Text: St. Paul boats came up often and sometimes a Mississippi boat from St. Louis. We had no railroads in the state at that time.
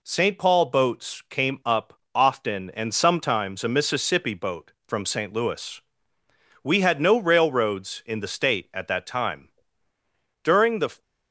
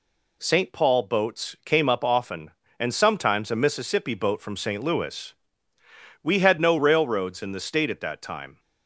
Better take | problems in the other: second | pauses between "up" and "often"; slight; at 1.9 s; 0.20 s long // goes on to say "During the"; from 10.4 s on; 0.58 s long

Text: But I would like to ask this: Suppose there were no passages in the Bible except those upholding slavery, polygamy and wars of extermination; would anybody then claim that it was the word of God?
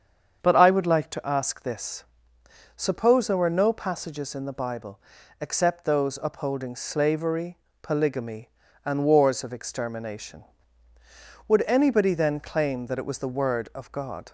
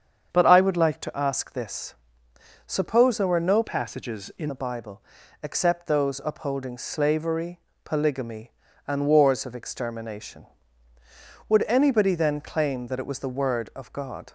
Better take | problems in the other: first | starts louder than the rest; strong; until 1.3 s; 7.5 dB; strong in the first // changes voice from "passages" to "in"; from 3.6 to 4.5 s; 0.9 s long // pauses between "Bible" and "except"; at 5.0 s; 0.40 s long; also in the first

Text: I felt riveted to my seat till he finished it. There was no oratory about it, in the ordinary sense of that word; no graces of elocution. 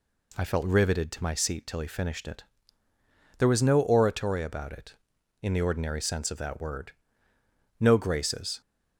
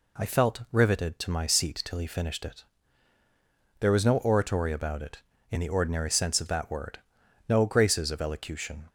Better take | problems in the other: second | stops before "of elocution"; at 8.6 s

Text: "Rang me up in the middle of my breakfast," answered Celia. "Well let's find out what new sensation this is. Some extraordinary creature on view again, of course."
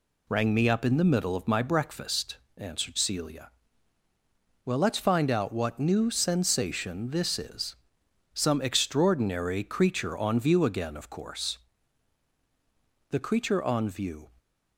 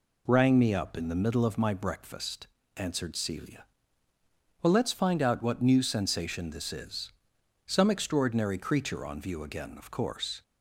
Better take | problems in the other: second | goes on to say "The creature on view"; noticeable; from 13.0 s on; 1.2 s long

